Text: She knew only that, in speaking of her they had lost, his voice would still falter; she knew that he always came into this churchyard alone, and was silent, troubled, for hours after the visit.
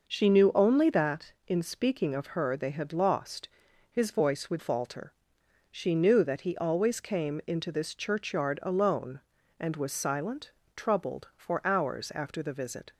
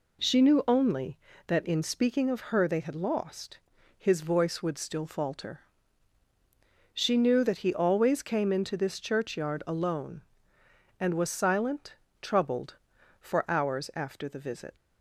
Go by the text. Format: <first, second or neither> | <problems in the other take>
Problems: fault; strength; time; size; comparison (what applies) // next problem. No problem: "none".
second | skips "still"; at 4.5 s